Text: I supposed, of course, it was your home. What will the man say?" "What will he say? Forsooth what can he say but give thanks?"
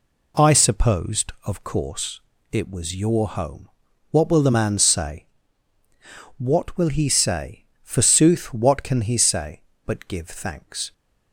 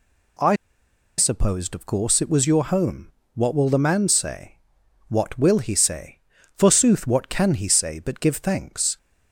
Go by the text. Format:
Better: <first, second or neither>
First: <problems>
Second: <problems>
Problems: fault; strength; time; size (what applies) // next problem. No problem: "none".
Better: first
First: none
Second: pauses between "I" and "supposed"; noticeable; at 0.5 s; 0.64 s long